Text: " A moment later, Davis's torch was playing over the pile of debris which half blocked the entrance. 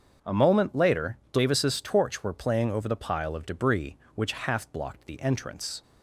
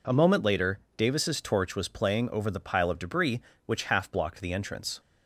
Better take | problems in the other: second | starts louder than the rest; until 1.3 s; 7 dB // says "were" for "was"; at 2.2 s

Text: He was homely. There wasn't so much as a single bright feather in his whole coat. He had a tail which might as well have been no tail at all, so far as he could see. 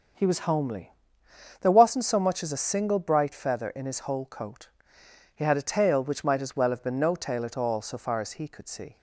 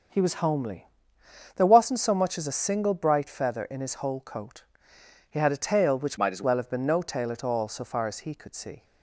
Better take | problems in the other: first | starts louder than the rest; strong; until 1.7 s; 7 dB; strong in the first // changes voice from "might" to "as"; from 6.1 to 6.4 s; 0.3 s long

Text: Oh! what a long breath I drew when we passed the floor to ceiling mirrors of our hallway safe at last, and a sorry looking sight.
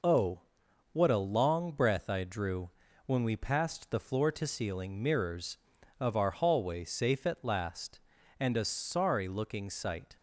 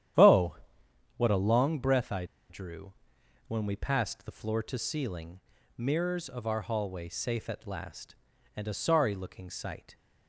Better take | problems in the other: first | starts louder than the rest; strong; until 1.7 s; 10.5 dB // pauses between "I" and "drew"; slight; at 2.2 s; 0.24 s long // pauses between "drew" and "when"; noticeable; at 2.9 s; 0.54 s long; also in the first // pauses between "ceiling" and "mirrors"; at 5.3 s; 0.40 s long

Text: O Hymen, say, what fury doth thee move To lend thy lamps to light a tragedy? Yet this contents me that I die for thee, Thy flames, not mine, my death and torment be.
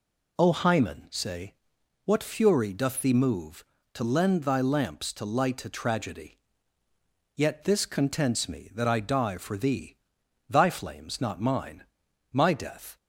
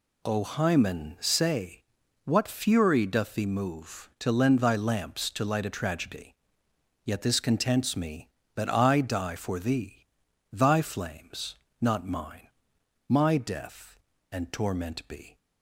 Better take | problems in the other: second | stops before "and torment be"; at 12.9 s

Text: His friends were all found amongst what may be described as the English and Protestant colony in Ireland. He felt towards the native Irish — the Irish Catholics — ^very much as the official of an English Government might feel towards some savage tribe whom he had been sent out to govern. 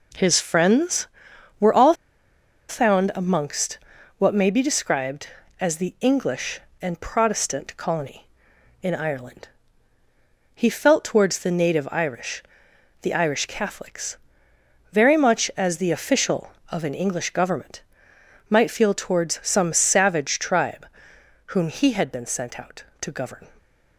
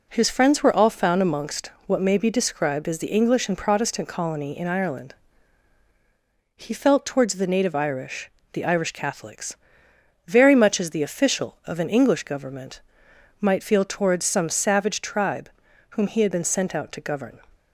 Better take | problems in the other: second | pauses between "all" and "found"; noticeable; at 1.9 s; 0.74 s long // pauses between "amongst" and "what"; at 3.7 s; 0.38 s long; slight in the second // pauses between "Government" and "might"; noticeable; at 17.8 s; 0.66 s long; noticeable in the second // pauses between "tribe" and "whom"; noticeable; at 20.8 s; 0.62 s long; also in the second

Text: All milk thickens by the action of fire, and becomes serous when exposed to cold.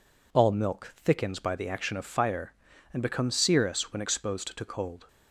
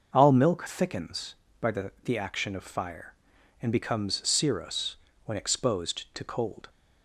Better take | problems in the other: first | starts louder than the rest; noticeable; until 1.1 s; 6 dB // says "the" twice; at 2.0 s // pauses between "serous" and "when"; slight; at 4.9 s; 0.30 s long

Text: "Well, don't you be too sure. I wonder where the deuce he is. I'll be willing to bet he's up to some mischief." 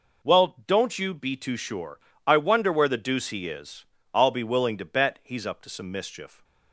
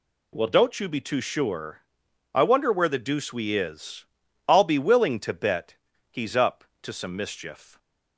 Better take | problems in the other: first | says "we" for "he"; at 3.3 s // pauses between "bet" and "he's"; slight; at 5.7 s; 0.34 s long

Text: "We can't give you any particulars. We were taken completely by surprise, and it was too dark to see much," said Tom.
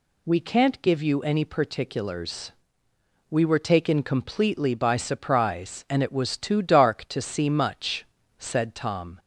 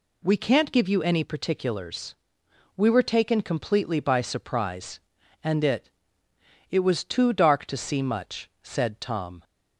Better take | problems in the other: first | says "it" twice; at 6.7 s

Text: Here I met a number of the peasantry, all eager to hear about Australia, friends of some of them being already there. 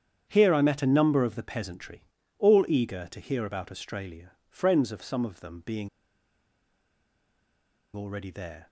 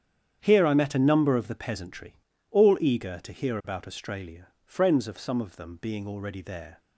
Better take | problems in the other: second | starts louder than the rest; strong; until 1.3 s; 9 dB; strong in the second // pauses between "being" and "already"; strong; at 5.8 s; 2.0 s long

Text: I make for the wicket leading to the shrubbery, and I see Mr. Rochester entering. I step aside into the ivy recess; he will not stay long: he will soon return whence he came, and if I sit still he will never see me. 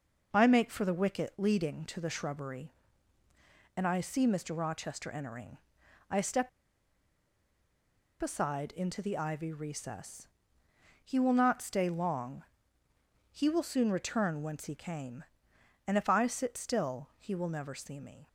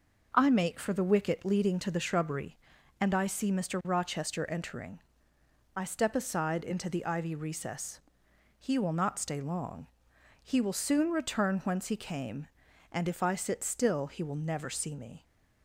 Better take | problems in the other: second | pauses between "step" and "aside"; strong; at 6.4 s; 1.7 s long

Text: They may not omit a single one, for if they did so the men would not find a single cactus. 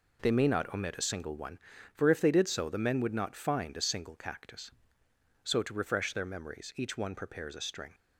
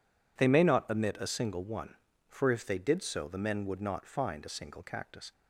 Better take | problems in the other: second | goes on to say "So to refresh their memories each one prepares a string"; strong; from 5.4 s on; 2.5 s long

